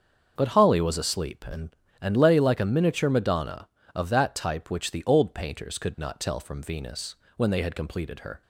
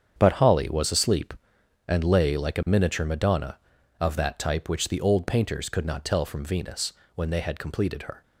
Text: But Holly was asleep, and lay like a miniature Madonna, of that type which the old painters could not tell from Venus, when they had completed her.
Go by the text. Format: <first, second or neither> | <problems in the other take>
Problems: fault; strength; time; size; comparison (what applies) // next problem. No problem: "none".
second | starts louder than the rest; until 1.3 s; 6.5 dB; strong in the second // says "and" twice; at 1.9 s